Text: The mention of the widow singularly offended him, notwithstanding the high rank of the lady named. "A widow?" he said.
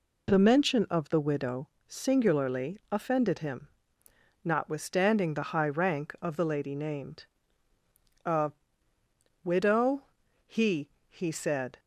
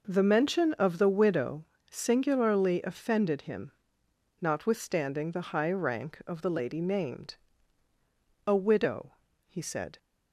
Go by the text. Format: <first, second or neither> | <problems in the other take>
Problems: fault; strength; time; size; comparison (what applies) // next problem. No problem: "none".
second | pauses between "widow" and "singularly"; slight; at 1.6 s; 0.18 s long; slight in the second // pauses between "A" and "widow"; noticeable; at 8.5 s; 0.92 s long // says "he" twice; at 11.0 s